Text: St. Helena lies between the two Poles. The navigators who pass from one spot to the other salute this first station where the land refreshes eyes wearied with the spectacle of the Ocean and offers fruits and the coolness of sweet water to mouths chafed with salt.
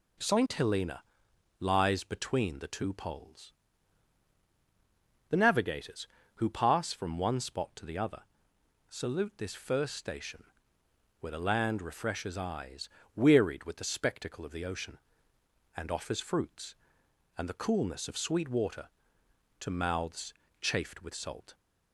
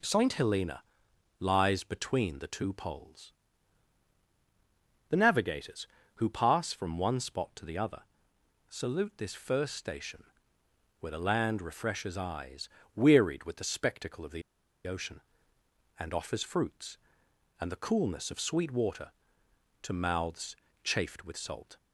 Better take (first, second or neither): first